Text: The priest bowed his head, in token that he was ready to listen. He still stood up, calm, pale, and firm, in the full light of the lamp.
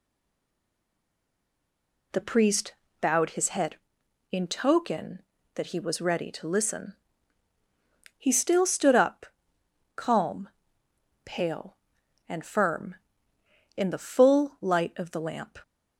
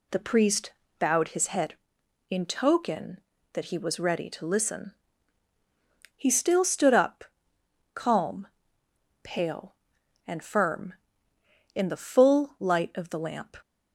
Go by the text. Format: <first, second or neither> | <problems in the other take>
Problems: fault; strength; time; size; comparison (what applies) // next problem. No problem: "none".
second | stays silent before the first word; until 2.1 s; 2.1 s long // pauses between "priest" and "bowed"; slight; at 2.7 s; 0.28 s long; slight in the second